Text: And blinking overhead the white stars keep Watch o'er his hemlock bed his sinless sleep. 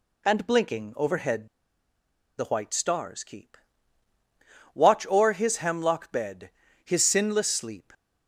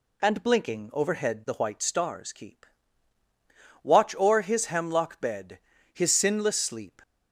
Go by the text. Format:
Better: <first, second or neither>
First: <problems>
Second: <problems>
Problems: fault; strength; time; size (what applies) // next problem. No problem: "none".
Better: second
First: pauses between "overhead" and "the"; noticeable; at 1.4 s; 0.90 s long // pauses between "keep" and "Watch"; at 3.5 s; 1.1 s long // pauses between "bed" and "his"; slight; at 6.4 s; 0.34 s long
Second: pauses between "keep" and "Watch"; at 2.6 s; 1.1 s long // pauses between "bed" and "his"; slight; at 5.5 s; 0.34 s long